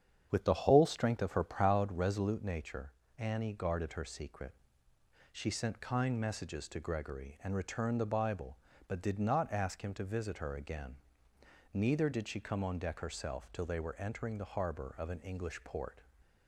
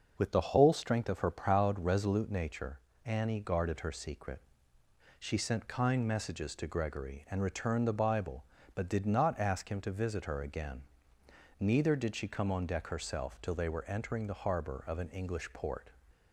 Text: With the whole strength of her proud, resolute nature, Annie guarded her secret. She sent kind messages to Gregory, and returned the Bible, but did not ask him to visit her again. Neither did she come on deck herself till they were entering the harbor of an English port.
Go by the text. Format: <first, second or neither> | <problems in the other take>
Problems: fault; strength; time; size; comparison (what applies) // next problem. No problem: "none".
second | starts louder than the rest; strong; until 2.0 s; 8 dB